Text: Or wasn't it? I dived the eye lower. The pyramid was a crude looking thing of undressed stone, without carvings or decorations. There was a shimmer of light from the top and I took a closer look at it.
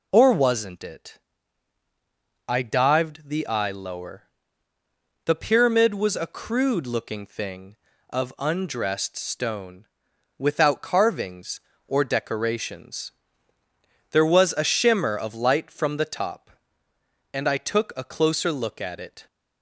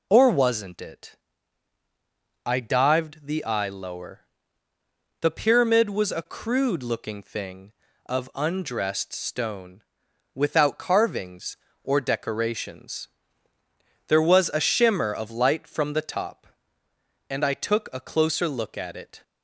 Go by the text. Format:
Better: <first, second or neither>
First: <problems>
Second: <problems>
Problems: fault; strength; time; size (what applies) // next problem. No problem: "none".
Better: neither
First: none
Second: none